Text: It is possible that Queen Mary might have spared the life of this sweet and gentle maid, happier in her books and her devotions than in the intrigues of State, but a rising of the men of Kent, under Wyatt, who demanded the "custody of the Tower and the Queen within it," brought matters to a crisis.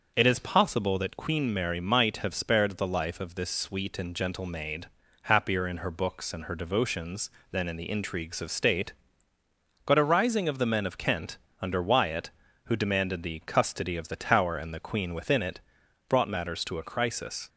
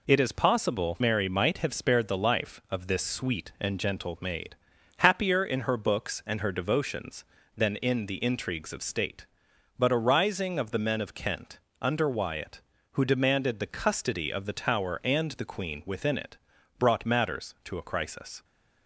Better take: first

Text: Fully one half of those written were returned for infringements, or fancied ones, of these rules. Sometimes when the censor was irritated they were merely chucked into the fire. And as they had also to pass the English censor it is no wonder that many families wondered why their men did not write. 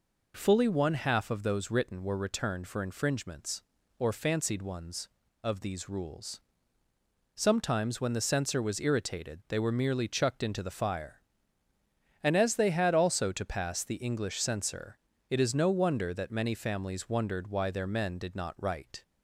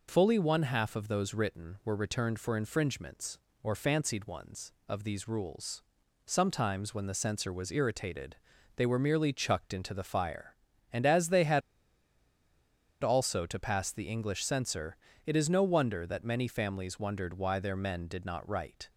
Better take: first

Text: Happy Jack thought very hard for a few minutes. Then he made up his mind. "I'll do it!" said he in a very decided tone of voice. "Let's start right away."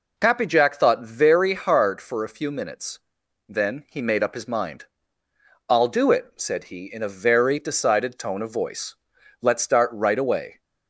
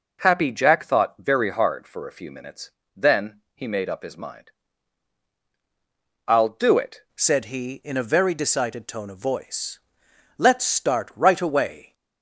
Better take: first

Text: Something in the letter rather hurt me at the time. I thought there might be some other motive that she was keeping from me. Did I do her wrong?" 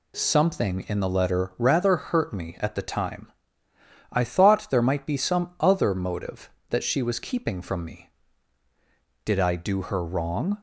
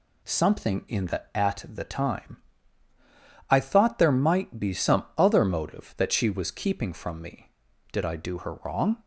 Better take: first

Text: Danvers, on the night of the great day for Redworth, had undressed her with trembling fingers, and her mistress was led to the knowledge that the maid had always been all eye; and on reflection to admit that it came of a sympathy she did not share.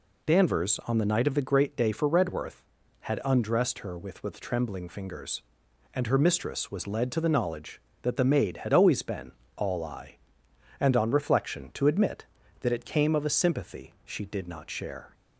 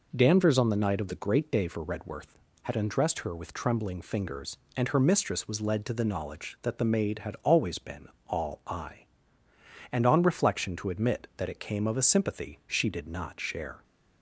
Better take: second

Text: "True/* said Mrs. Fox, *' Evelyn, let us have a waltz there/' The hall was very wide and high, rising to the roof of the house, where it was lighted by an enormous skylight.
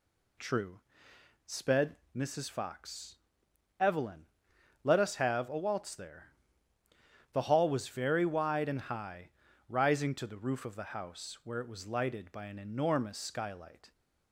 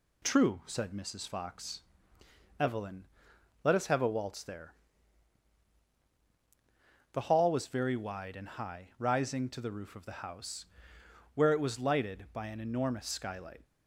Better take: second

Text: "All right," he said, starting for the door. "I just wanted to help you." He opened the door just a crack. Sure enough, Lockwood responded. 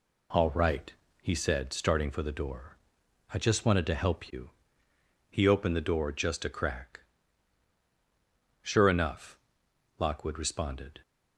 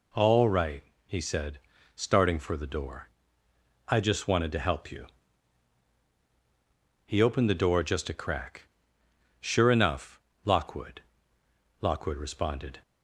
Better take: first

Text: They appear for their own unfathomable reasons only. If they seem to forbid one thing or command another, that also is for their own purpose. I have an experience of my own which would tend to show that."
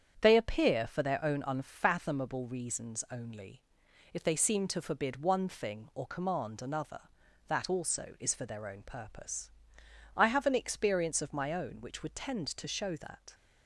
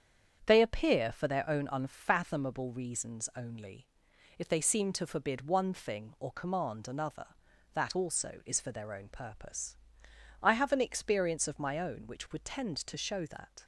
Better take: neither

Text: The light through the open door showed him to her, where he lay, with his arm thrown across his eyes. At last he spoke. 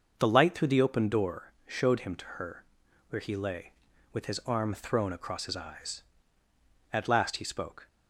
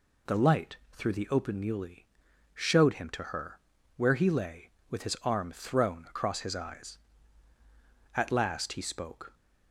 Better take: first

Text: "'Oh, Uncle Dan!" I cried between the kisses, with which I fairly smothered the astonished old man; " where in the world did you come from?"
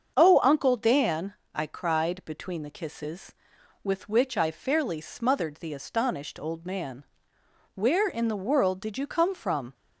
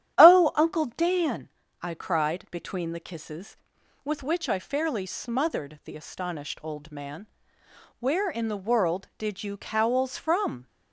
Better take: first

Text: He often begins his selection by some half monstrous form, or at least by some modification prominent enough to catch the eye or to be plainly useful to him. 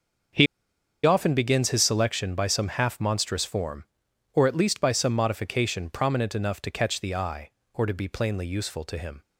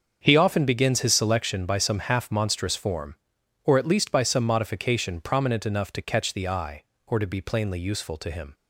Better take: second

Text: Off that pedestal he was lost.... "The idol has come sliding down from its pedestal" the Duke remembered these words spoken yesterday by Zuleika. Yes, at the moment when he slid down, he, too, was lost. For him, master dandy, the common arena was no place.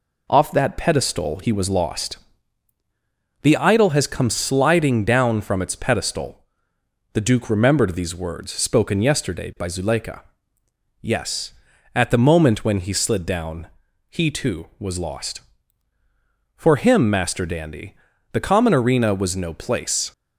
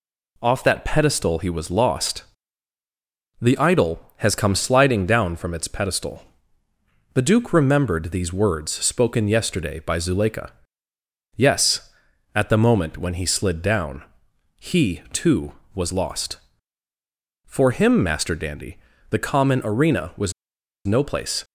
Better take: first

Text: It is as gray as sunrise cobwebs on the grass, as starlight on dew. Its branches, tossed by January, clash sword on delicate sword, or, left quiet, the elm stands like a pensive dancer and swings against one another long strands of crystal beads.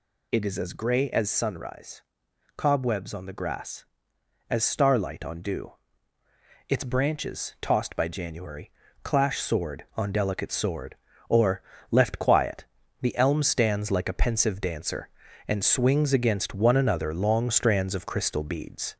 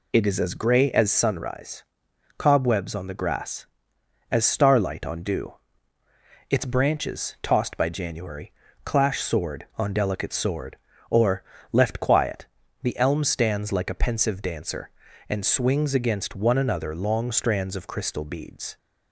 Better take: second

